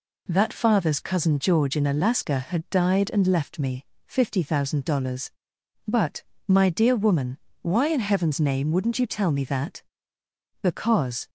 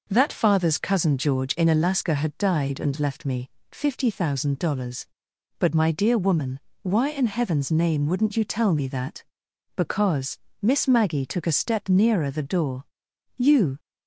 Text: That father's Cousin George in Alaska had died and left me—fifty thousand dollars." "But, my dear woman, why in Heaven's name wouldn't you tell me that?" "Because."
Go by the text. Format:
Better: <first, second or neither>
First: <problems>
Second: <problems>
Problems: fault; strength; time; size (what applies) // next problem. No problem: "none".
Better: first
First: none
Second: goes on to say "Miss Maggie took a step nearer the door You"; strong; from 10.6 s on; 3.1 s long